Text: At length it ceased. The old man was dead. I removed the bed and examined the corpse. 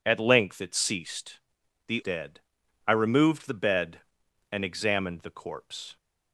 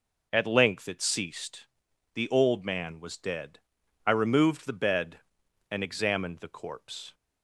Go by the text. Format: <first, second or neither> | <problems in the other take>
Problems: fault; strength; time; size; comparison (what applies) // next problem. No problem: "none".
second | skips "old man was"; at 2.0 s